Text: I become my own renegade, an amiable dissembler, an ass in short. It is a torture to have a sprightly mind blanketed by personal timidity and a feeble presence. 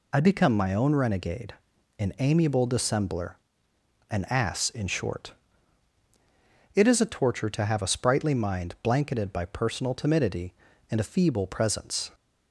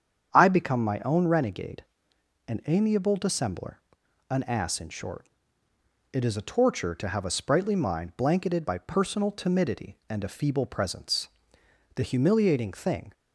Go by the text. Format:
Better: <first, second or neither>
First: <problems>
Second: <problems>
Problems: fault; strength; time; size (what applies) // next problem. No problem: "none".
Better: first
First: none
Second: starts louder than the rest; strong; until 1.3 s; 8 dB // goes on to say "The humiliating thing"; noticeable; from 11.9 s on; 1.1 s long